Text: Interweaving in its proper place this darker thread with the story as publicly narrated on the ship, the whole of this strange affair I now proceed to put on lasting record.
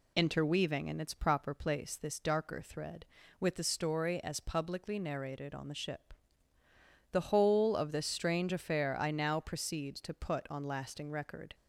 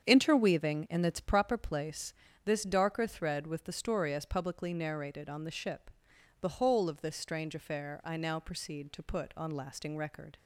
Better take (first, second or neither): first